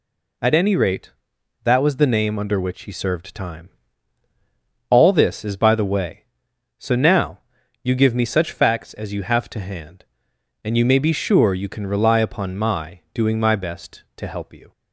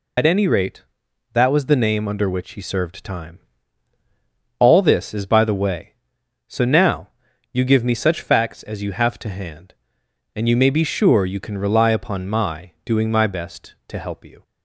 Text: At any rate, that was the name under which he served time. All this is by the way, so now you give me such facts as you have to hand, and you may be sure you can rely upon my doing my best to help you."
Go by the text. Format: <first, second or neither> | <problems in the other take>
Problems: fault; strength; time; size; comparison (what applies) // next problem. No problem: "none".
first | loses the start of "At"; at 0.1 s; 65 ms // pauses between "now" and "you"; at 7.0 s; 0.44 s long; also in the first